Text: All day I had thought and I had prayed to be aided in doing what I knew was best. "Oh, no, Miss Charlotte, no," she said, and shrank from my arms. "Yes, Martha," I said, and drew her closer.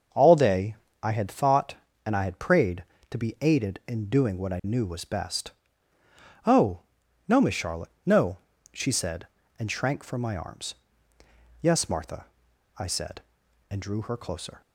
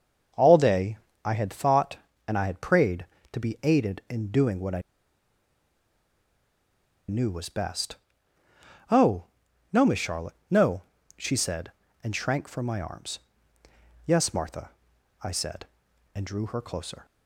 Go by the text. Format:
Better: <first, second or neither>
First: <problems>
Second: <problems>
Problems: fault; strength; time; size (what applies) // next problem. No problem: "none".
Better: first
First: starts louder than the rest; until 1.4 s; 6 dB // pauses between "day" and "I"; slight; at 0.7 s; 0.28 s long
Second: starts louder than the rest; until 1.6 s; 6 dB // pauses between "day" and "I"; slight; at 0.9 s; 0.28 s long // pauses between "I" and "knew"; strong; at 4.8 s; 2.2 s long